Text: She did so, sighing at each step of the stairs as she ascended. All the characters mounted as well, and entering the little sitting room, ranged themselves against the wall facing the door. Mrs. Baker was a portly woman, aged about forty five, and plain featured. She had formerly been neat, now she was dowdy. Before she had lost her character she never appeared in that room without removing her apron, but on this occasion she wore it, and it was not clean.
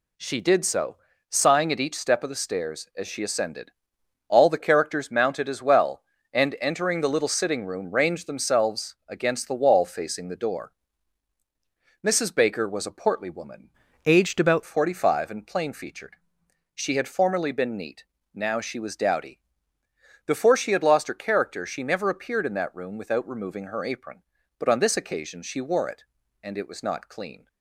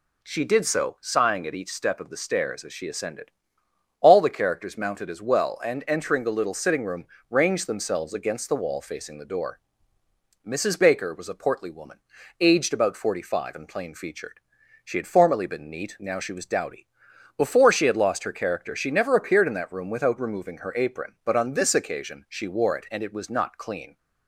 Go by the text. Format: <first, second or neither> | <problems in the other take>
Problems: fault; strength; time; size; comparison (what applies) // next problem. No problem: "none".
second | changes voice from "aged" to "about"; from 14.0 to 14.6 s; 0.6 s long